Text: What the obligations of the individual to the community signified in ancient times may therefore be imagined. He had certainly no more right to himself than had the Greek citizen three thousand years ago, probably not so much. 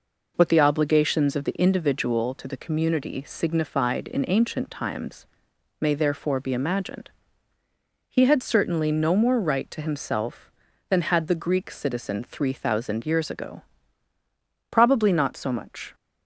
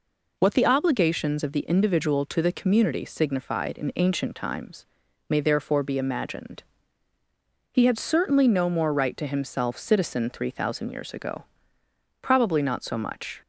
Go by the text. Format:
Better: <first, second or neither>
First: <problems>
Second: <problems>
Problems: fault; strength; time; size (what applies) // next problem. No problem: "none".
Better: first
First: pauses between "times" and "may"; noticeable; at 5.2 s; 0.52 s long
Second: pauses between "times" and "may"; at 4.8 s; 0.42 s long // skips "than had the Greek"; at 9.7 s